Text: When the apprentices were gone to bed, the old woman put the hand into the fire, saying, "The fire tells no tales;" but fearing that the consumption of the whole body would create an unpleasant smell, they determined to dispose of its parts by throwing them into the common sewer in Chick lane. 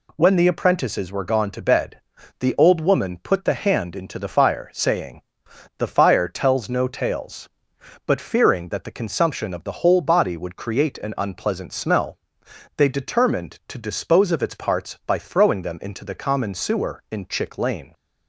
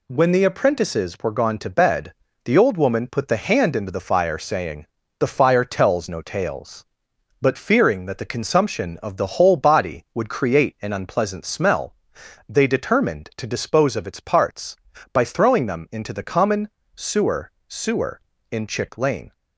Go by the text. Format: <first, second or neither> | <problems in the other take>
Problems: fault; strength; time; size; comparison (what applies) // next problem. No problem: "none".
first | pauses between "common" and "sewer"; slight; at 16.6 s; 0.26 s long // says "sewer" twice; at 17.6 s